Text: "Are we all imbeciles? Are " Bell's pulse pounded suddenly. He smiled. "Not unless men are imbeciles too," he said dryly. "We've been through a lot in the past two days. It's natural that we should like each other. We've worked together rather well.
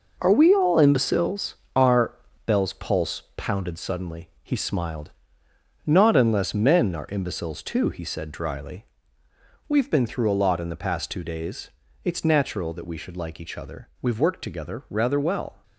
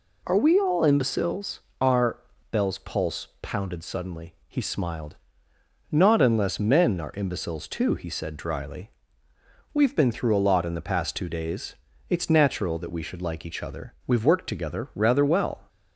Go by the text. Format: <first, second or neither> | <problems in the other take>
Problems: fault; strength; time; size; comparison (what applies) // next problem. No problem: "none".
second | gets quieter; strong; throughout; 7.5 dB